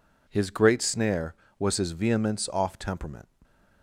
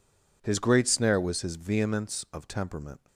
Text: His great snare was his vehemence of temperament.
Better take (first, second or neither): second